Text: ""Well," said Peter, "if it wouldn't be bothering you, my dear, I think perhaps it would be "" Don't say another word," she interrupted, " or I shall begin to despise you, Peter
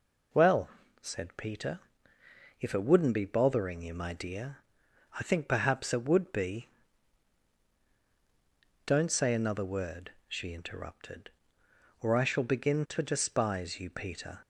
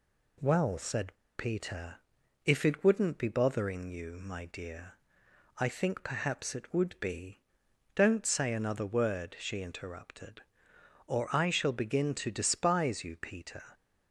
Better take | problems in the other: first | pauses between "said" and "Peter"; slight; at 1.1 s; 0.22 s long

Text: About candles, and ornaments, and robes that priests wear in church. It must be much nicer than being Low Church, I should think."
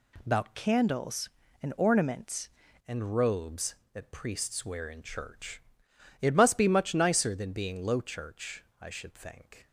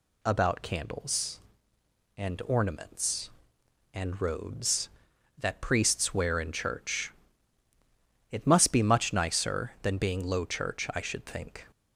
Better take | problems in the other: second | changes voice from "candles" to "ornaments"; from 0.5 to 2.5 s; 2.0 s long

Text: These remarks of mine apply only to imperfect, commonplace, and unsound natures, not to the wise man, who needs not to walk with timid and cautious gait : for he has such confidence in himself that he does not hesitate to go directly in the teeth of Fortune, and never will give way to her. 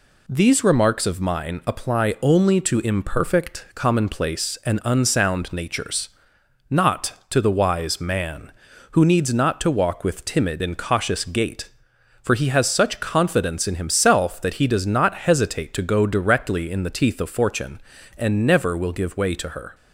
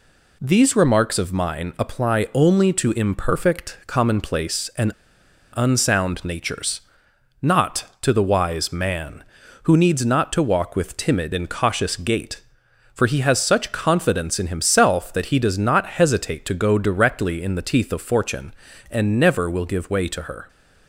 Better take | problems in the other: first | pauses between "and" and "unsound"; noticeable; at 4.9 s; 0.62 s long

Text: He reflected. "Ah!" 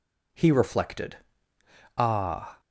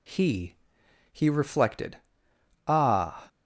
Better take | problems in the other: first | says "He" twice; at 1.1 s

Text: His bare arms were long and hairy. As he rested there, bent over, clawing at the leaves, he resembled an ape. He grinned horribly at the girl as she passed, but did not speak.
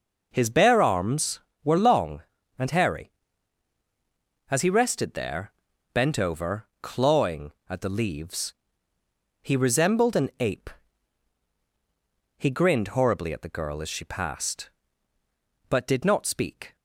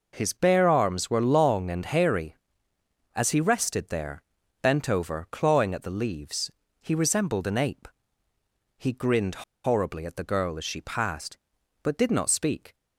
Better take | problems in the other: first | pauses between "grinned" and "horribly"; slight; at 9.4 s; 0.22 s long

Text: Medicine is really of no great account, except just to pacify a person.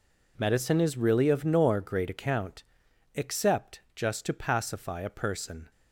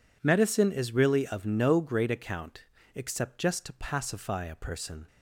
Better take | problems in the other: second | says "nor" for "no"; at 1.4 s

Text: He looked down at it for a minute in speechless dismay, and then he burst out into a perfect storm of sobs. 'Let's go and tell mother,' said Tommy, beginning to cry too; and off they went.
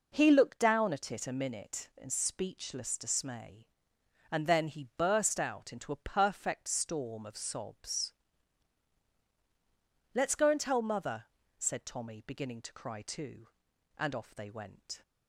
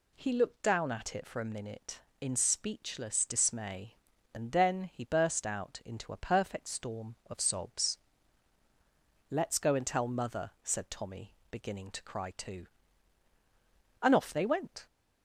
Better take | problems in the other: second | skips "for"; at 1.2 s

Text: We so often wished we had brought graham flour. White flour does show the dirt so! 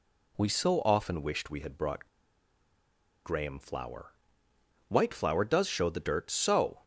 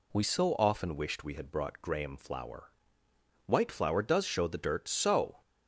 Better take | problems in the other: second | pauses between "brought" and "graham"; at 2.0 s; 1.1 s long

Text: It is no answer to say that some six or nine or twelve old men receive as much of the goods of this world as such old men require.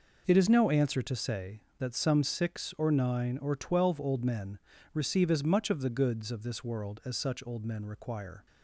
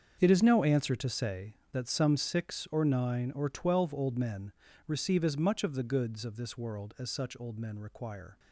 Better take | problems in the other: first | gets quieter; strong; throughout; 14 dB // pauses between "men" and "receive"; slight; at 4.5 s; 0.34 s long; slight in the first

